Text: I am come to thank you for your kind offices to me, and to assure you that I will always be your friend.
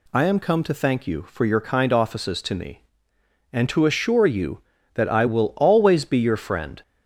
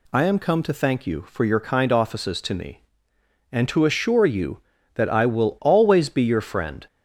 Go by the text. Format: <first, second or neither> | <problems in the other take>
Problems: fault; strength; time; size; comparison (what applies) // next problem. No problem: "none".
neither | none